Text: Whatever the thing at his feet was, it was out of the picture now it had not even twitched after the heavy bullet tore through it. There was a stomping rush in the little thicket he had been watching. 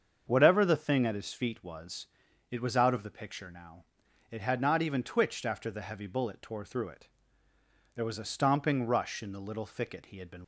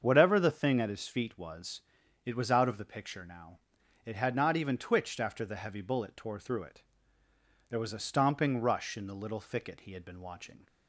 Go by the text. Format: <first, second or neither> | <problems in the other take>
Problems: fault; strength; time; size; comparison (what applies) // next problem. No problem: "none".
second | starts louder than the rest; until 1.2 s; 7 dB; also in the second // pauses between "now" and "it"; noticeable; at 3.8 s; 0.46 s long; noticeable in the second // stops before "watching"; at 10.4 s